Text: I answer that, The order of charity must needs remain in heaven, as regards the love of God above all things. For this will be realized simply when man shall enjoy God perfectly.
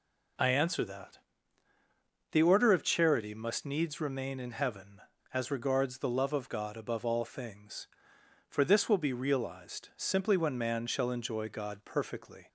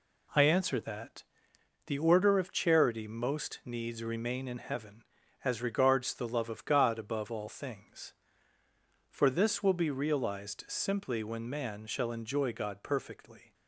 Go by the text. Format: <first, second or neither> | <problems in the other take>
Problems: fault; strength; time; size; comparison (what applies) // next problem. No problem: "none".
first | says "most" for "must"; at 3.0 s